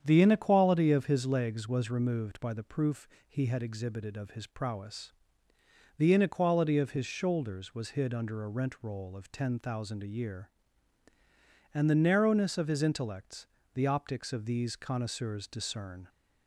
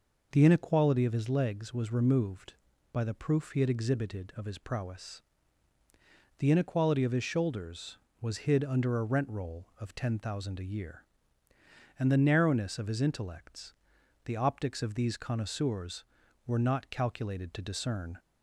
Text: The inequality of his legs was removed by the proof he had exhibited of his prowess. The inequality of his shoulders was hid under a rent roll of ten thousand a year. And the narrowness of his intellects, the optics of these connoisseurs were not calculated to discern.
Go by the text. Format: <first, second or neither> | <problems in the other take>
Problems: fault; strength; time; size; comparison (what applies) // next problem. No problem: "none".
second | starts louder than the rest; strong; until 1.0 s; 8.5 dB // pauses between "proof" and "he"; slight; at 3.0 s; 0.22 s long // skips "were not calculated to"; at 15.4 s